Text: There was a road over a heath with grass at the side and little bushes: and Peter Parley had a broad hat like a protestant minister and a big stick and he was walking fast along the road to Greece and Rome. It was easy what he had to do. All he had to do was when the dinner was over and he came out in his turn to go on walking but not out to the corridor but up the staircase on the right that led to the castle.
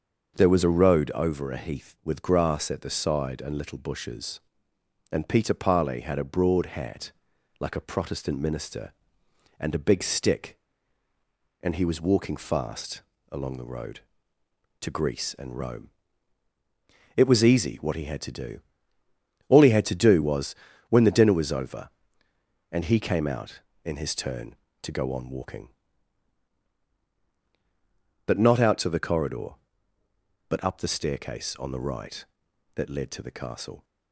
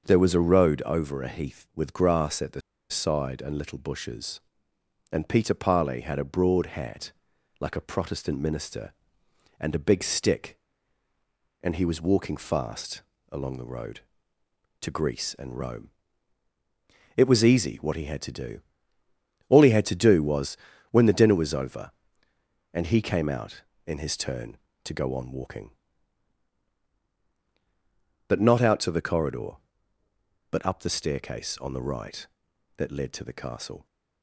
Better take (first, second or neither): first